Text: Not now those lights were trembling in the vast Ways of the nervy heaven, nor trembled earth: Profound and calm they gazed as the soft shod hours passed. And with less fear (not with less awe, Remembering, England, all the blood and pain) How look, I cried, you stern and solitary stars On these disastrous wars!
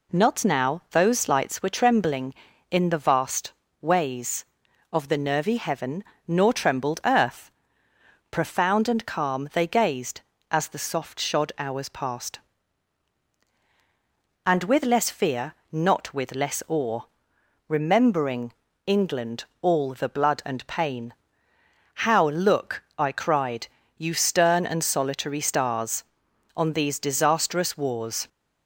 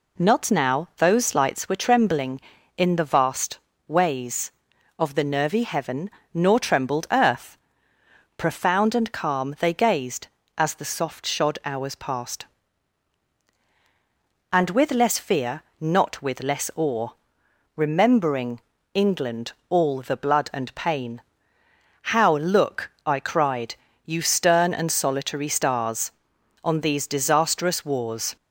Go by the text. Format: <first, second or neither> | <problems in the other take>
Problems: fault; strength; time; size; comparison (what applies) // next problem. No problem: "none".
neither | pauses between "vast" and "Ways"; slight; the same in both